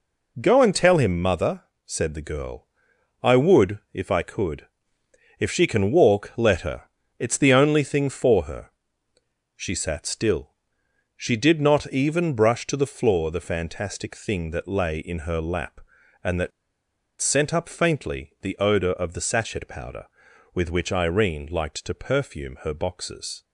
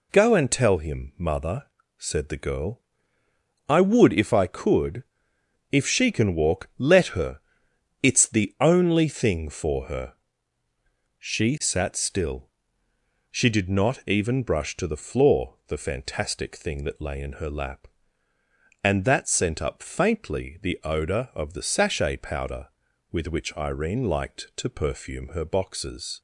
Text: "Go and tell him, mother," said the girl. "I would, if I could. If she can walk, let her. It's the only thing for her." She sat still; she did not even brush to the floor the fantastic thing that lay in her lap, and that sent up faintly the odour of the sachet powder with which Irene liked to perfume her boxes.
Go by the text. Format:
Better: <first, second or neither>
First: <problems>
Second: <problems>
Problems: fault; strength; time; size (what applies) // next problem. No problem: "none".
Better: second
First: pauses between "that" and "sent"; noticeable; at 16.5 s; 0.70 s long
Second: none